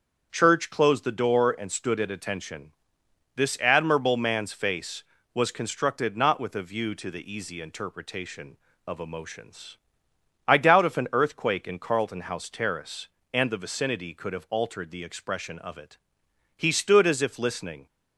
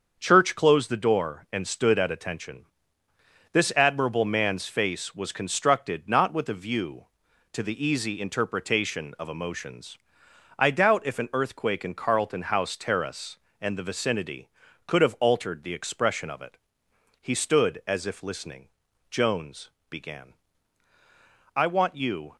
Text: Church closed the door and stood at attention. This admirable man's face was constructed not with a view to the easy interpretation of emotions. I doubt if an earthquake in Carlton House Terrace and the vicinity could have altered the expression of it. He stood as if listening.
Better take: first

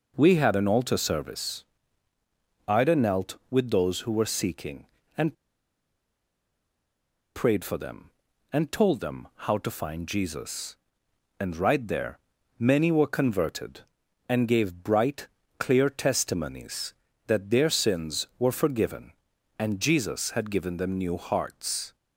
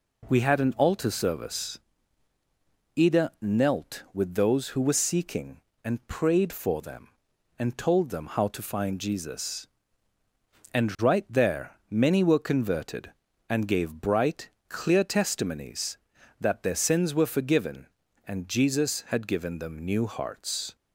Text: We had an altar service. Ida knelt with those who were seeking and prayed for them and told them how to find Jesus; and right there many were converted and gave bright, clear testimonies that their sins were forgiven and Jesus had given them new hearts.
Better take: second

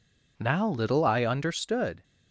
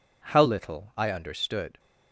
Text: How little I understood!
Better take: second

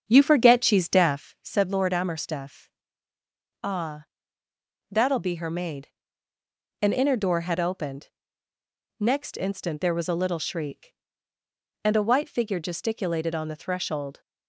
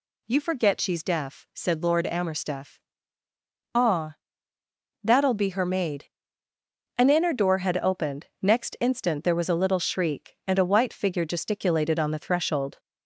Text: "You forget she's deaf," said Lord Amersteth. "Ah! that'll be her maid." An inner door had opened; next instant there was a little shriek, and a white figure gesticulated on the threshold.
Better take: second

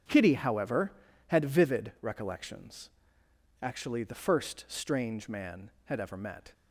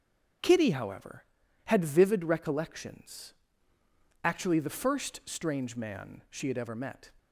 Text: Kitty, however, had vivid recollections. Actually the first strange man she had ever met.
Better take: second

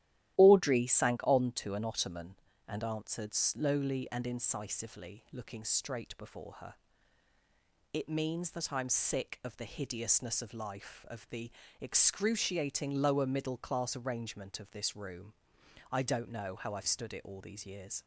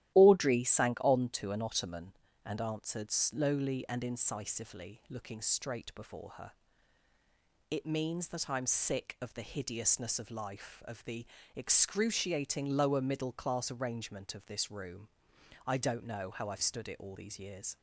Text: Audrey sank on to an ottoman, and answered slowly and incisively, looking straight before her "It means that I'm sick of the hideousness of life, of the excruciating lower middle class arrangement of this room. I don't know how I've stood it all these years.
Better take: neither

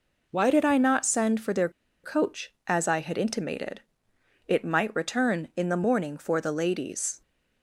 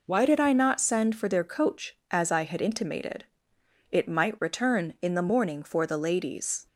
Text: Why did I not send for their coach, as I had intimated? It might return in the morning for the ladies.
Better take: second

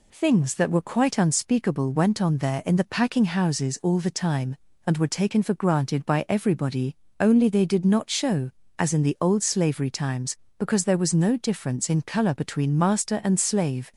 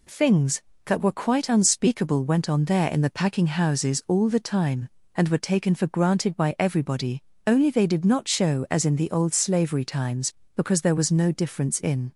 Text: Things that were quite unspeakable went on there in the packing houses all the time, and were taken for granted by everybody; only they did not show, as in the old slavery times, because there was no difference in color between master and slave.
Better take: first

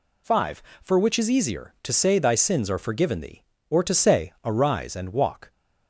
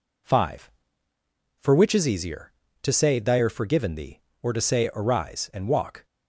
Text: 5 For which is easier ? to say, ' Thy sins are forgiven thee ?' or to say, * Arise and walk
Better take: first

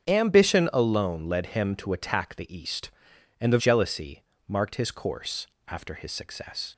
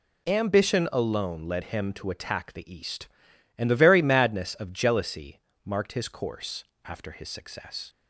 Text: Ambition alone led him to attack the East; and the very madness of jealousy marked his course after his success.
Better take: second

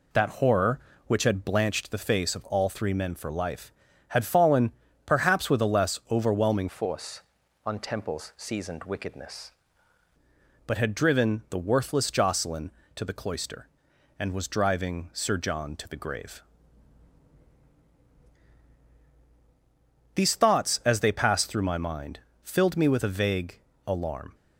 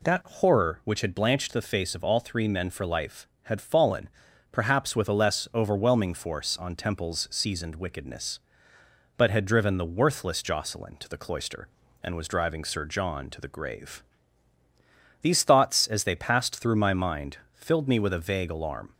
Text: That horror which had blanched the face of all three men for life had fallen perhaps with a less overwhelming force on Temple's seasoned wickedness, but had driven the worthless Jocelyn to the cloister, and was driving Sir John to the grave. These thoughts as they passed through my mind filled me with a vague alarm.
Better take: second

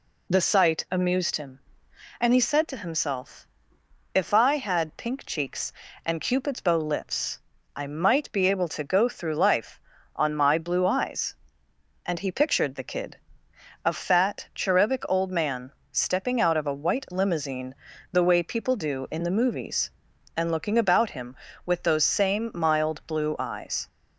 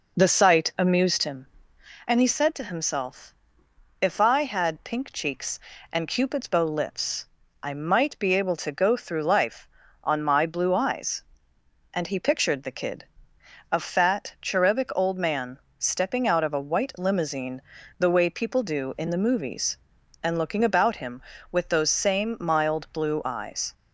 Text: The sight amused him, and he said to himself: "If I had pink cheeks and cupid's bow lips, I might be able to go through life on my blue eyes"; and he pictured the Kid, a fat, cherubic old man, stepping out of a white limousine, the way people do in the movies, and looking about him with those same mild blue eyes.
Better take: first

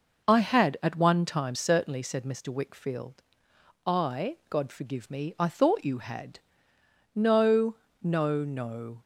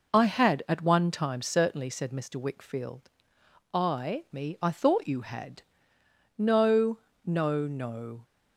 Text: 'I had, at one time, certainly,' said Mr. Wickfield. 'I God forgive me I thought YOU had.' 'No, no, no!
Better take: first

